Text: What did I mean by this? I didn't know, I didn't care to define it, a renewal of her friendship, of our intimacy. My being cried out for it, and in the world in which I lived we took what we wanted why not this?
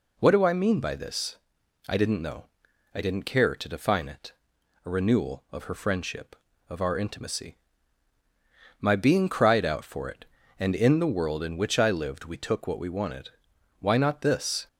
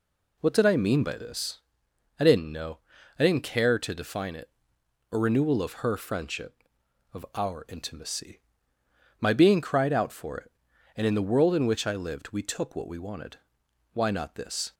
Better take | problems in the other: second | says "do" for "did"; at 0.3 s // pauses between "wanted" and "why"; noticeable; at 13.2 s; 0.50 s long; noticeable in the second

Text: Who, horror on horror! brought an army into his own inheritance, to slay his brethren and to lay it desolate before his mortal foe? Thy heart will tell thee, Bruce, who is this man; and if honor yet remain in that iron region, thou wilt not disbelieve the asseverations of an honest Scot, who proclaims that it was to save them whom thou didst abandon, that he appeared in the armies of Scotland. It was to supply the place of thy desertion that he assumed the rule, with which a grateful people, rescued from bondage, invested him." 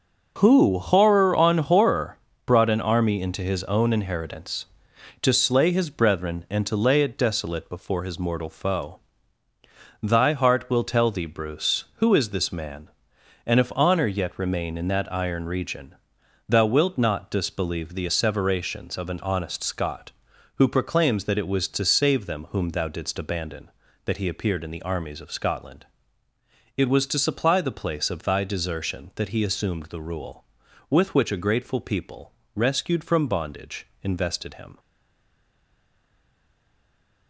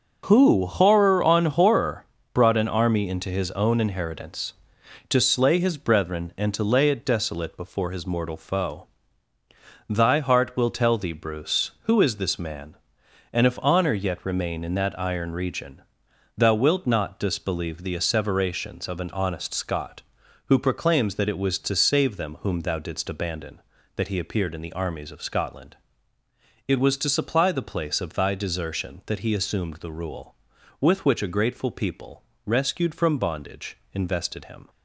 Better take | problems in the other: second | stays silent after the last word; strong; from 34.7 s on; 2.5 s long

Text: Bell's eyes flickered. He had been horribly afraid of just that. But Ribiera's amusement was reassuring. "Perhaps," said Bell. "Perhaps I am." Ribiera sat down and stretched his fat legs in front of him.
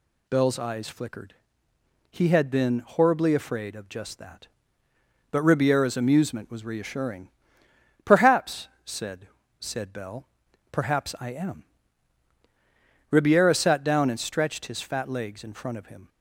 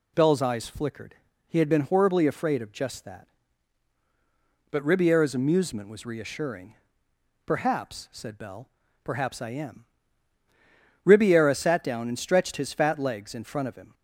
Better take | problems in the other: second | says "said" twice; at 9.6 s

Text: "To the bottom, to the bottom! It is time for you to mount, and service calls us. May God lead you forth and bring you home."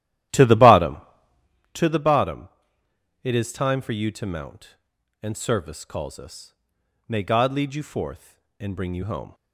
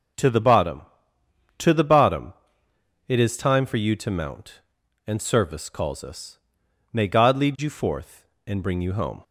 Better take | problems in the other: second | starts louder than the rest; strong; until 1.6 s; 13 dB

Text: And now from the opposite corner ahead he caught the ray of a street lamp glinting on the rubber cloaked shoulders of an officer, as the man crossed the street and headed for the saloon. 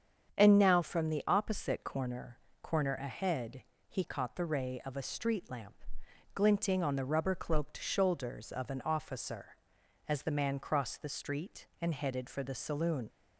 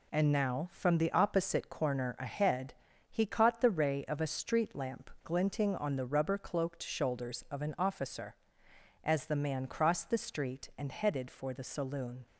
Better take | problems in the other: second | starts louder than the rest; strong; until 1.4 s; 7.5 dB // says "corner" twice; at 2.6 s // pauses between "ahead" and "he"; slight; at 3.6 s; 0.26 s long; slight in the second // pauses between "lamp" and "glinting"; noticeable; at 5.7 s; 0.60 s long

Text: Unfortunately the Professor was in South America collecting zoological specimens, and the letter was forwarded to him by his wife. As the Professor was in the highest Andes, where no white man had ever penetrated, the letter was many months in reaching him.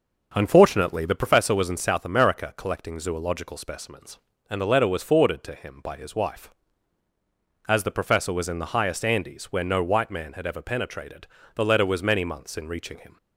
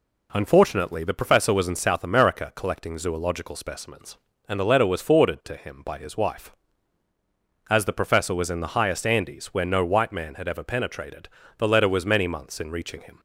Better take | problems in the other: second | starts louder than the rest; noticeable; until 1.5 s; 6 dB

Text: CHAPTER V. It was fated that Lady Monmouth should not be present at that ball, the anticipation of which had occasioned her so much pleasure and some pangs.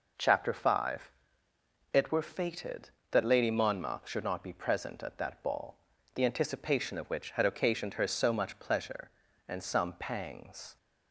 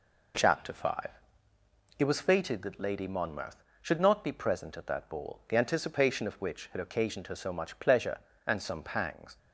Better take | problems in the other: second | says "were" for "was"; at 2.1 s

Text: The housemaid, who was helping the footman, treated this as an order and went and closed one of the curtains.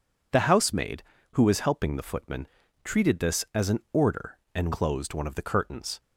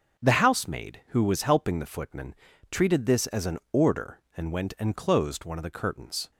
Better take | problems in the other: second | skips "went and"; at 4.7 s

